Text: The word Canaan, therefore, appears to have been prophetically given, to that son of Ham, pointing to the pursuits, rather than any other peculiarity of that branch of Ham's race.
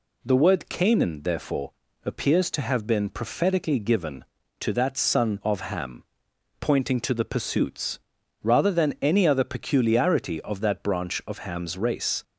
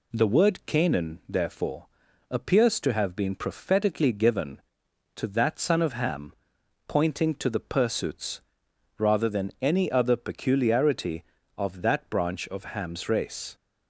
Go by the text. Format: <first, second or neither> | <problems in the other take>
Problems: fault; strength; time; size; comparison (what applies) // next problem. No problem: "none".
neither | none